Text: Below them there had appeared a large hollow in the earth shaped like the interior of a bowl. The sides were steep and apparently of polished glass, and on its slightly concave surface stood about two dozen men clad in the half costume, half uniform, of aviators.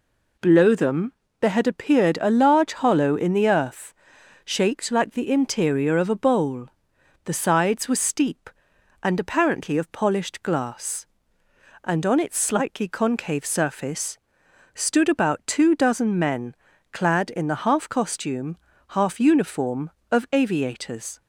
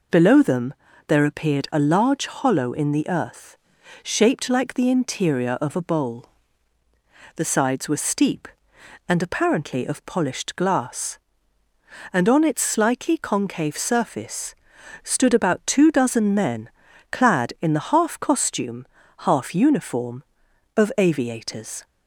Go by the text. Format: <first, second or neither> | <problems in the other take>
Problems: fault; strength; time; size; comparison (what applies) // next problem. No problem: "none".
first | pauses between "them" and "there"; slight; at 0.7 s; 0.32 s long; slight in the first // skips "had"; at 1.2 s // pauses between "earth" and "shaped"; noticeable; at 3.5 s; 0.46 s long; noticeable in the first // pauses between "surface" and "stood"; noticeable; at 14.5 s; 0.48 s long; noticeable in the first // pauses between "men" and "clad"; at 16.6 s; 0.42 s long; slight in the first